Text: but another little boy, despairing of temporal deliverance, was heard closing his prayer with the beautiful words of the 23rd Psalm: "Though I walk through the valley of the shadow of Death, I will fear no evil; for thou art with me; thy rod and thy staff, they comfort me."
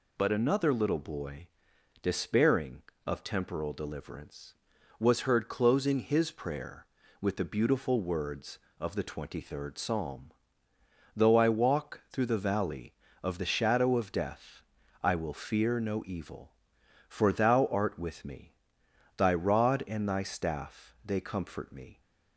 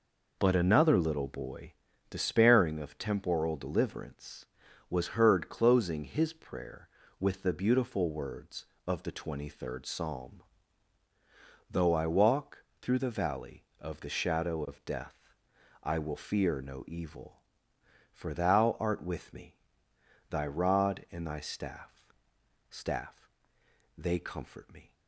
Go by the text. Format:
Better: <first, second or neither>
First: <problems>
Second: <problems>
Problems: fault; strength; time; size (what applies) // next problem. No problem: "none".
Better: first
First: none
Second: pauses between "walk" and "through"; slight; at 12.6 s; 0.18 s long // says "staff" twice; at 22.6 s